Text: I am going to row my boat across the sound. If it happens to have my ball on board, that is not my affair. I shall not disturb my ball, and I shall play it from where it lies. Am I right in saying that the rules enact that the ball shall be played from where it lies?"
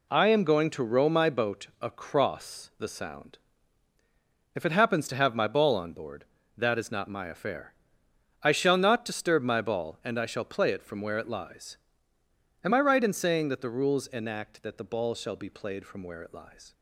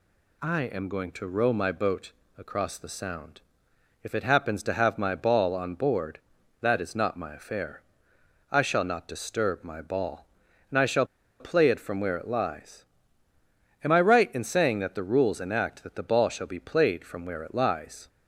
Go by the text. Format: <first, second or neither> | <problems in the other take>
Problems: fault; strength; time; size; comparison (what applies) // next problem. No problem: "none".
first | pauses between "boat" and "across"; slight; at 2.1 s; 0.24 s long // pauses between "shall" and "play"; slight; at 11.0 s; 0.35 s long